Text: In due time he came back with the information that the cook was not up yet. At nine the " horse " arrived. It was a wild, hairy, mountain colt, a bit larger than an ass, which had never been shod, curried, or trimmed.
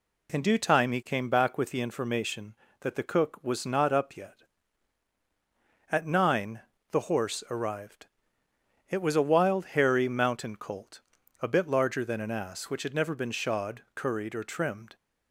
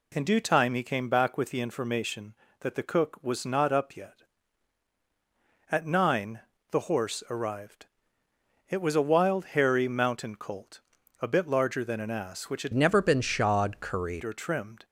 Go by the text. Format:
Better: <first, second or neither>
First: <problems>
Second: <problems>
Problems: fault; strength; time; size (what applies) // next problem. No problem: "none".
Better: first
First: pauses between "nine" and "the"; slight; at 6.6 s; 0.28 s long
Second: pauses between "nine" and "the"; slight; at 6.4 s; 0.28 s long // changes voice from "never" to "curried"; from 12.7 to 14.2 s; 1.5 s long